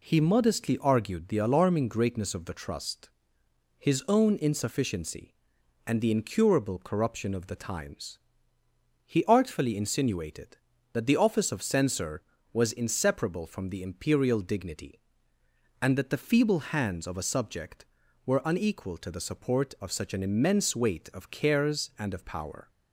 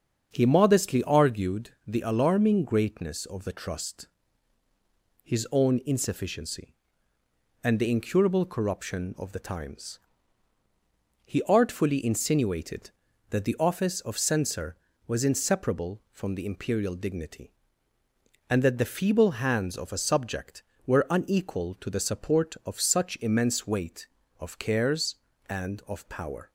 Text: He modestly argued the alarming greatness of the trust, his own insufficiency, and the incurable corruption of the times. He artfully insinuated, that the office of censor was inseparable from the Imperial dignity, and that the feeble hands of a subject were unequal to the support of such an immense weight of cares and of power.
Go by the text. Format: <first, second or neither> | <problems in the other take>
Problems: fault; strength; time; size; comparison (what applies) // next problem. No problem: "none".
first | starts louder than the rest; until 1.3 s; 7 dB // skips "an"; at 23.1 s